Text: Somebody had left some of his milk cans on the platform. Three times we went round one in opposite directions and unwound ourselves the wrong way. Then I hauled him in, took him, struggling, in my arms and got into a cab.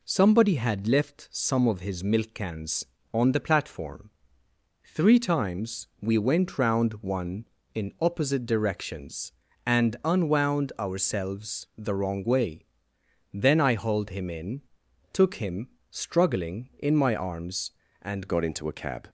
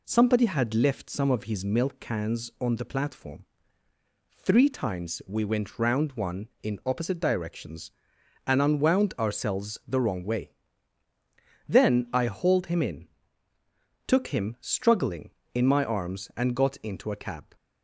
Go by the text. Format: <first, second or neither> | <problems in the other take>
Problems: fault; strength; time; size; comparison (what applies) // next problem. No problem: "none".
second | changes voice at "got"; from 18.2 s on; 0.8 s long